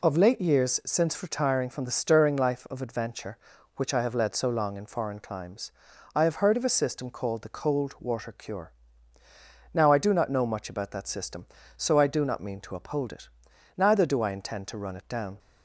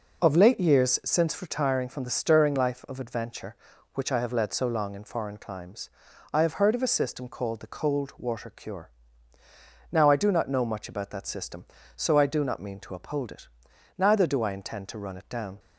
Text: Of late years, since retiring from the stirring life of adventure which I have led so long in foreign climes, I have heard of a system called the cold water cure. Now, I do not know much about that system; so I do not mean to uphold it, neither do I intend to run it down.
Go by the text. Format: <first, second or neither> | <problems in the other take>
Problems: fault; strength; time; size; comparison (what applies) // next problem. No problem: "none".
first | starts louder than the rest; noticeable; until 1.3 s; 5 dB